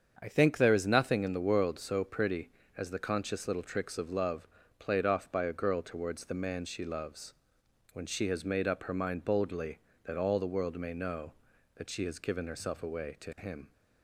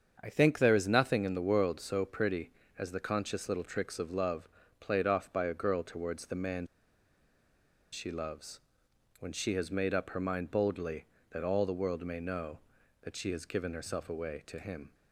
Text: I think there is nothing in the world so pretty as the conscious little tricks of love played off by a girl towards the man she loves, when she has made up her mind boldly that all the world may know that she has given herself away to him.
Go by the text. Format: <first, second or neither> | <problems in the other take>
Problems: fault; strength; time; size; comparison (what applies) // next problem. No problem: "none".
first | starts louder than the rest; until 1.2 s; 7 dB; also in the first // pauses between "love" and "played"; slight; at 4.4 s; 0.32 s long; slight in the first // pauses between "man" and "she"; strong; at 6.6 s; 1.2 s long